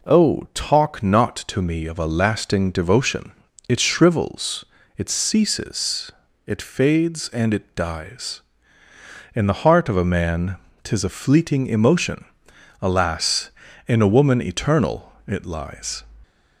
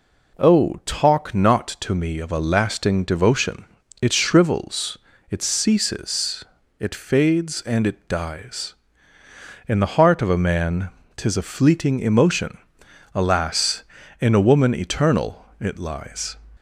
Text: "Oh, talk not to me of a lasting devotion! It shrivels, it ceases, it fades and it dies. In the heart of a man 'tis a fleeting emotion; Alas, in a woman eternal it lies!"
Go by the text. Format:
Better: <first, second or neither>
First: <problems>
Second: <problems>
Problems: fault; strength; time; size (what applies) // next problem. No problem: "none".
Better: neither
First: pauses between "man" and "tis"; slight; at 10.5 s; 0.28 s long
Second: pauses between "man" and "tis"; slight; at 10.8 s; 0.28 s long